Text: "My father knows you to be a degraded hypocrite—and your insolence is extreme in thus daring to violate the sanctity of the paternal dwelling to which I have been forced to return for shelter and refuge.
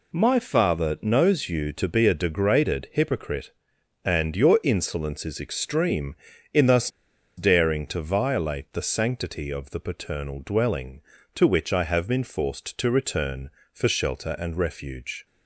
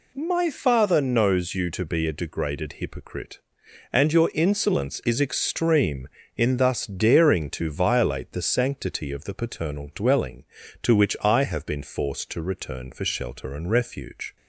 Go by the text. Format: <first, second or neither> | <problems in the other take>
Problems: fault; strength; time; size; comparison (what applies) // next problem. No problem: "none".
second | pauses between "thus" and "daring"; noticeable; at 6.9 s; 0.47 s long